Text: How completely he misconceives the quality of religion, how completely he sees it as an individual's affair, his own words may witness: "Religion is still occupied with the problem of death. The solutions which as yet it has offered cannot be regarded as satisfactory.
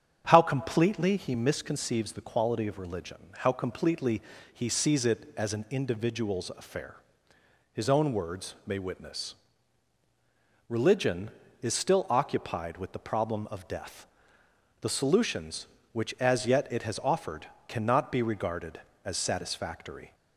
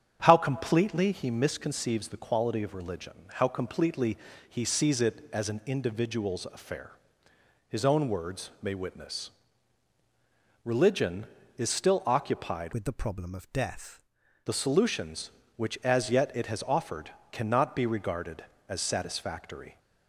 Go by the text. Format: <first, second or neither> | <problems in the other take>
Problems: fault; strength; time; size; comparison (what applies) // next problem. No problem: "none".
first | starts louder than the rest; strong; until 1.2 s; 8 dB; strong in the first // pauses between "completely" and "he"; slight; at 4.1 s; 0.28 s long; slight in the first // changes voice from "with" to "death"; from 12.7 to 14.0 s; 1.3 s long // pauses between "offered" and "cannot"; slight; at 17.1 s; 0.20 s long; slight in the first